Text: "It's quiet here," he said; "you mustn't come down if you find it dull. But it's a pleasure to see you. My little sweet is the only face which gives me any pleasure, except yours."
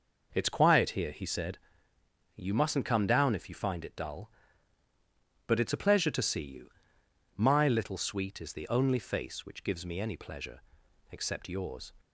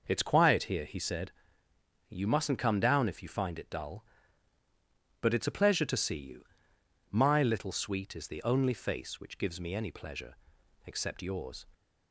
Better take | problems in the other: neither | none

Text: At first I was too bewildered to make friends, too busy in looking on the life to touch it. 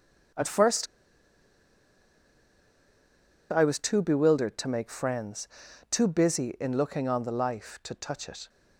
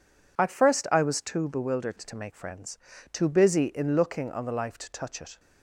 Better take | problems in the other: second | starts louder than the rest; strong; until 3.9 s; 7 dB // pauses between "first" and "I"; strong; at 0.8 s; 2.6 s long

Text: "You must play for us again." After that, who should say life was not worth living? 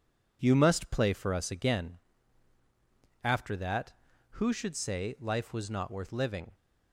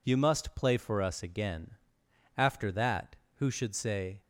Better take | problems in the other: first | stops before "life was not worth living"; at 4.2 s

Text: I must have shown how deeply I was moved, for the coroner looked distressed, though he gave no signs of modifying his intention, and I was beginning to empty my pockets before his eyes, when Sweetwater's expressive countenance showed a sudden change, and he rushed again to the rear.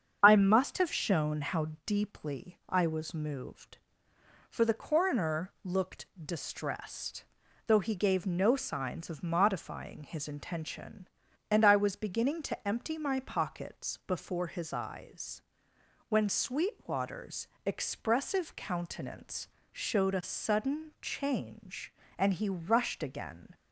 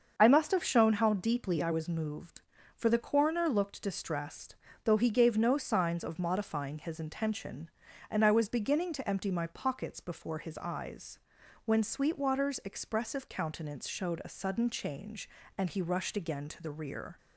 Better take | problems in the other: second | starts louder than the rest; strong; until 1.2 s; 7.5 dB; also in the second // pauses between "how" and "deeply"; slight; at 1.6 s; 0.18 s long // pauses between "looked" and "distressed"; slight; at 6.0 s; 0.16 s long // pauses between "Sweetwater's" and "expressive"; slight; at 17.4 s; 0.18 s long // pauses between "countenance" and "showed"; slight; at 19.4 s; 0.24 s long // stops before "to the rear"; at 23.5 s

